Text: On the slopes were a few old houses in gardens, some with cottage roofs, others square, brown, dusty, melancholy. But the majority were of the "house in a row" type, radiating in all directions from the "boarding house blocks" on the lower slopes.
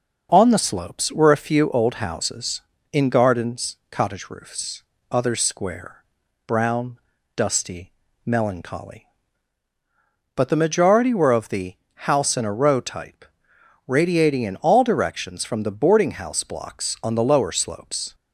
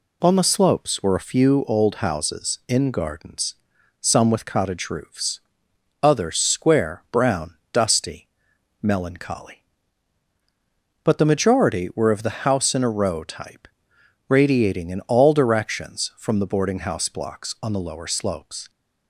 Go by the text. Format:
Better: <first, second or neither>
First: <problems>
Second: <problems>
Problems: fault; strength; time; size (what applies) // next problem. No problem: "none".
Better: second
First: skips "some with"; at 3.8 s // pauses between "the" and "house"; slight; at 11.7 s; 0.32 s long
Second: none